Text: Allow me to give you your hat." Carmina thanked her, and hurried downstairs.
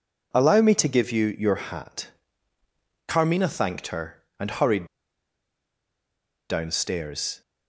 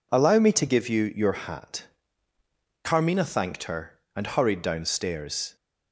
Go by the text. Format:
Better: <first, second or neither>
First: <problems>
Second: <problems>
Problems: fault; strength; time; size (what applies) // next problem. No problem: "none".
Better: second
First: pauses between "hurried" and "downstairs"; strong; at 4.8 s; 1.6 s long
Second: none